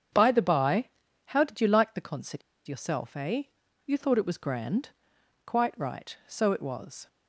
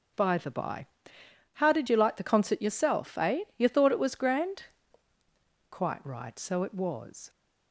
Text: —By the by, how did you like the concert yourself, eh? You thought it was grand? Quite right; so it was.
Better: second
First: starts louder than the rest; strong; until 1.5 s; 8 dB // pauses between "concert" and "yourself"; slight; at 2.4 s; 0.26 s long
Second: none

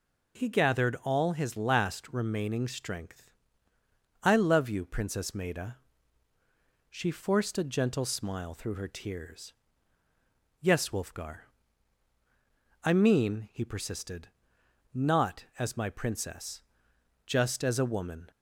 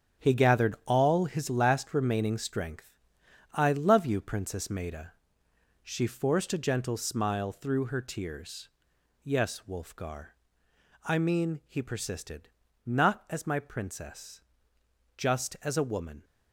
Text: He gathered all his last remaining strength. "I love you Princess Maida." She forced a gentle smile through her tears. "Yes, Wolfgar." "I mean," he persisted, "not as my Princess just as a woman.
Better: first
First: pauses between "Princess" and "just"; noticeable; at 16.6 s; 0.64 s long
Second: gets quieter; strong; throughout; 9 dB // pauses between "Princess" and "just"; noticeable; at 14.4 s; 0.74 s long

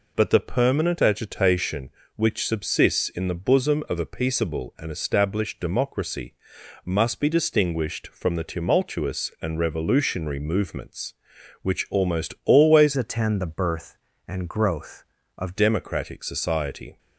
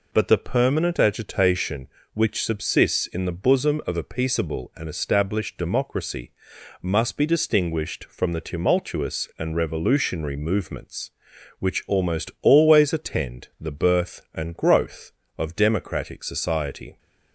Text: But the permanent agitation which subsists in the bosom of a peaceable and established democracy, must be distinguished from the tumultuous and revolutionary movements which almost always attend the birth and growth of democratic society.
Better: second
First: changes voice from "attend" to "of"; from 12.9 to 15.5 s; 2.6 s long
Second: none

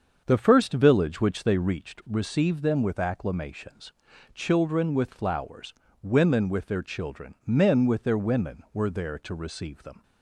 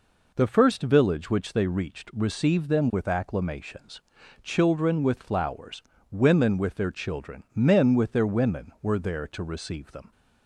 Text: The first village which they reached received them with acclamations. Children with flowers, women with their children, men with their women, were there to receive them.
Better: second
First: starts louder than the rest; until 1.9 s; 7 dB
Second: none

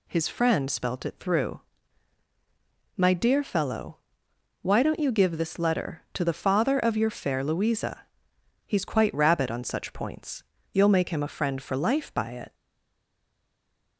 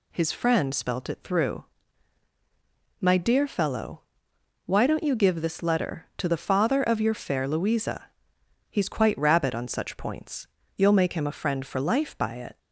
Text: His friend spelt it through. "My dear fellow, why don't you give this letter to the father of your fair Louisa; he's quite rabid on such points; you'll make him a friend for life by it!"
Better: second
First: stays silent after the last word; noticeable; from 12.5 s on; 1.4 s long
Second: none

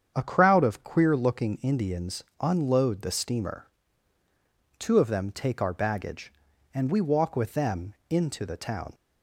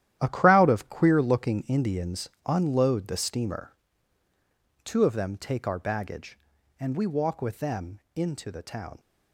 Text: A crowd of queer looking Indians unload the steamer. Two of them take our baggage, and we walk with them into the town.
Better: first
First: starts louder than the rest; strong; until 1.1 s; 8 dB // pauses between "Indians" and "unload"; slight; at 2.2 s; 0.16 s long // pauses between "them" and "into"; slight; at 7.9 s; 0.16 s long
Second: gets quieter; strong; throughout; 11 dB // starts louder than the rest; strong; until 1.2 s; 11.5 dB // pauses between "Indians" and "unload"; slight; at 2.2 s; 0.16 s long // pauses between "them" and "into"; slight; at 8.0 s; 0.16 s long

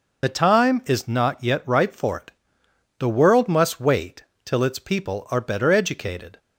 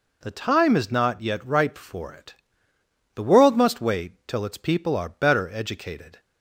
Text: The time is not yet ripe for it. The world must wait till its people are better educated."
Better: second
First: loses the start of "The"; at 0.2 s; 50 ms // pauses between "wait" and "till"; slight; at 4.2 s; 0.22 s long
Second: none

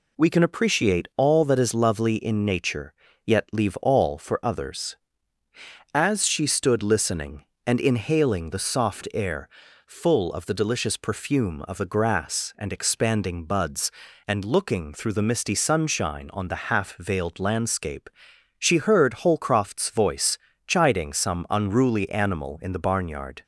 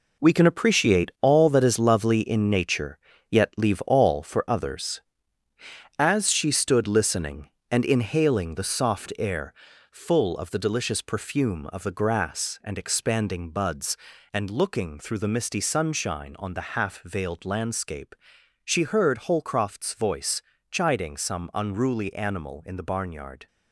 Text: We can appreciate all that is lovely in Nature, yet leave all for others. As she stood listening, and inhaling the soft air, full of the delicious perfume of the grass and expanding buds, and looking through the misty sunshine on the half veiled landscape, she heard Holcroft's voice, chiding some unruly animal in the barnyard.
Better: first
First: none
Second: gets quieter; strong; throughout; 9 dB

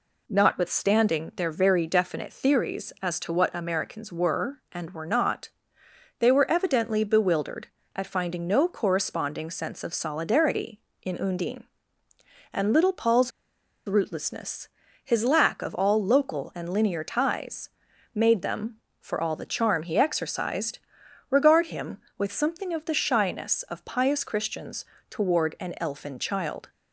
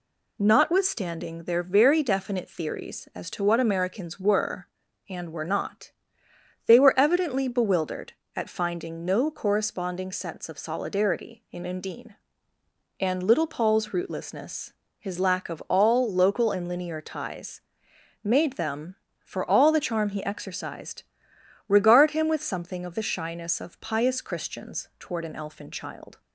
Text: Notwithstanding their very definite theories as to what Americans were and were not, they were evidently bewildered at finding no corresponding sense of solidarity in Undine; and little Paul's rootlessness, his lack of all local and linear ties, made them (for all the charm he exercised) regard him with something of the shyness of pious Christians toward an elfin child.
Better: second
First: pauses between "Paul's" and "rootlessness"; noticeable; at 13.3 s; 0.56 s long // pauses between "Christians" and "toward"; slight; at 24.8 s; 0.28 s long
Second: none

